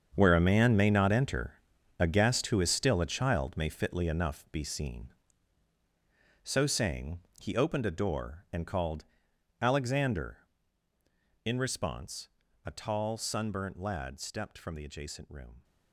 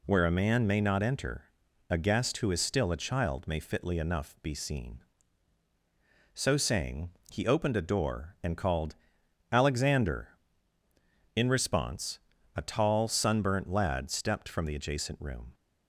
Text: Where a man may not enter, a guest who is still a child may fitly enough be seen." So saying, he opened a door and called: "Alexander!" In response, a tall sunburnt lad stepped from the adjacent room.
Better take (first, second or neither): second